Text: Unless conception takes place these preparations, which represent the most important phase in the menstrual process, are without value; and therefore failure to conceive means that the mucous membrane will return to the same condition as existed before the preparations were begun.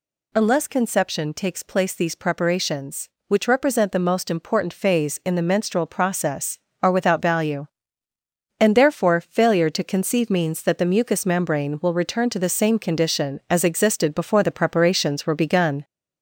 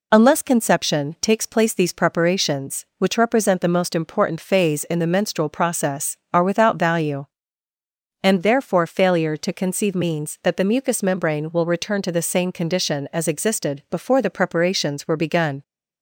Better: second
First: gets louder; throughout; 4 dB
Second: none

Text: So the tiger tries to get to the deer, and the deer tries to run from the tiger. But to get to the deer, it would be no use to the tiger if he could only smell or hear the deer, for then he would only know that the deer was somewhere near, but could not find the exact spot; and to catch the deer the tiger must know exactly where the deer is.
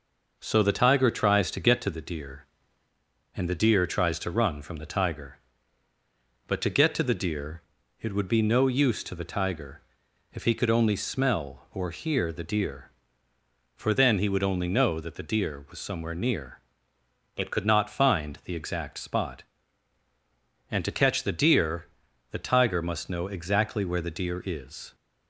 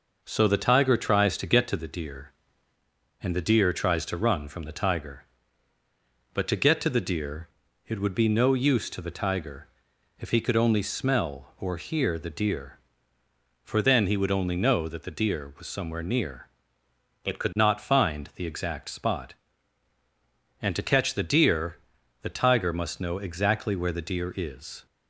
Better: neither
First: pauses between "tiger" and "if"; noticeable; at 9.8 s; 0.52 s long // pauses between "deer" and "the"; at 21.8 s; 0.44 s long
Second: pauses between "tiger" and "if"; noticeable; at 9.6 s; 0.52 s long // pauses between "deer" and "the"; at 21.7 s; 0.44 s long

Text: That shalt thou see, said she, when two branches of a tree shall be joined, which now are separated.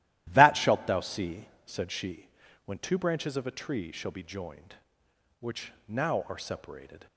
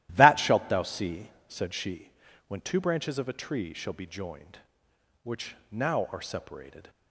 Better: neither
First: starts louder than the rest; strong; until 1.3 s; 14 dB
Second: starts louder than the rest; strong; until 1.1 s; 14 dB

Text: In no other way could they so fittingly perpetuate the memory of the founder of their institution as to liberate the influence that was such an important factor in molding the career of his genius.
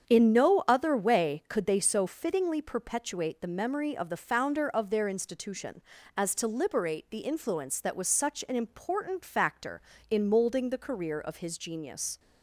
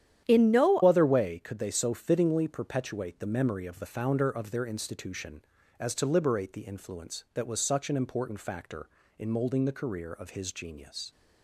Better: first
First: starts louder than the rest; strong; until 1.1 s; 8 dB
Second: starts louder than the rest; strong; until 1.2 s; 10 dB // changes voice at "other"; from 0.8 s on; 10.3 s long

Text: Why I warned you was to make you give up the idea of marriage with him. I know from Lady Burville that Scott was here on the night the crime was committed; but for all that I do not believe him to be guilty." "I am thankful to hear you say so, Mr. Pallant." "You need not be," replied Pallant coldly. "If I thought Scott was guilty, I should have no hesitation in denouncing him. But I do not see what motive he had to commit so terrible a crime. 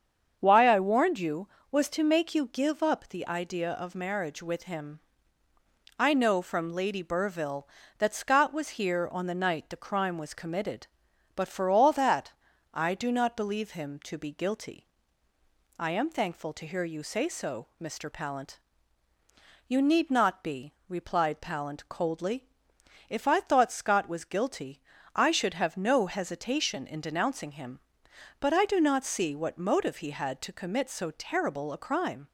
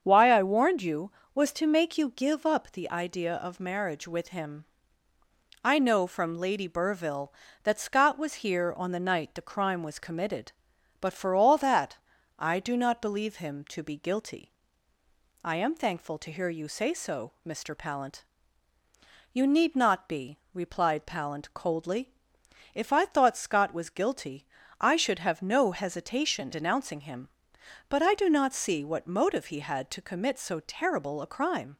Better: first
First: starts louder than the rest; strong; until 1.4 s; 7 dB // pauses between "that" and "I"; at 12.3 s; 0.38 s long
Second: starts louder than the rest; strong; until 1.0 s; 7.5 dB // pauses between "that" and "I"; at 11.9 s; 0.38 s long // skips "in"; at 26.5 s

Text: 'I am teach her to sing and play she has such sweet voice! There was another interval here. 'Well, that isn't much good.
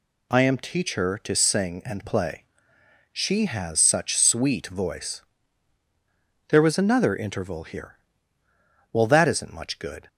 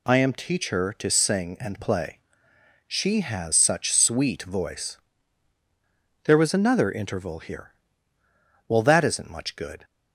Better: neither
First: pauses between "play" and "she"; noticeable; at 2.4 s; 0.72 s long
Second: pauses between "play" and "she"; noticeable; at 2.1 s; 0.72 s long

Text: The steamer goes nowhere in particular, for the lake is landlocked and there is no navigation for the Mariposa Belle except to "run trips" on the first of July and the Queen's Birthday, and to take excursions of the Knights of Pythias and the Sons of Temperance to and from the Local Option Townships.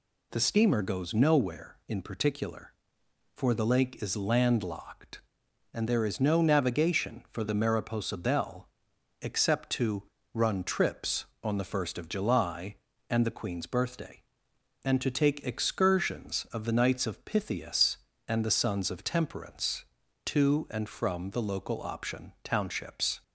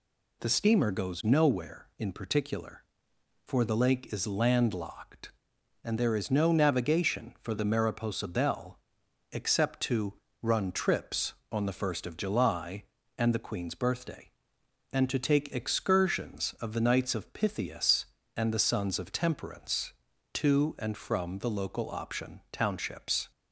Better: neither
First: pauses between "Belle" and "except"; noticeable; at 8.6 s; 0.54 s long // pauses between "to" and "run"; slight; at 10.0 s; 0.28 s long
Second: pauses between "Belle" and "except"; noticeable; at 8.7 s; 0.54 s long // pauses between "to" and "run"; slight; at 10.1 s; 0.26 s long

